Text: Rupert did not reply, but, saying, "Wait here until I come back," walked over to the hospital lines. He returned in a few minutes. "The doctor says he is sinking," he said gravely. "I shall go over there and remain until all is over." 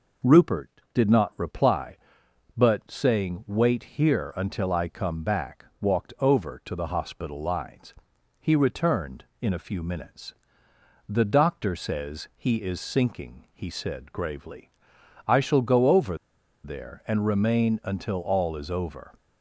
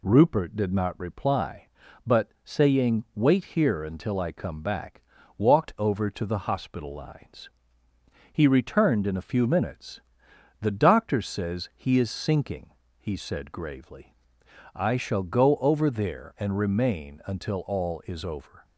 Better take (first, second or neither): second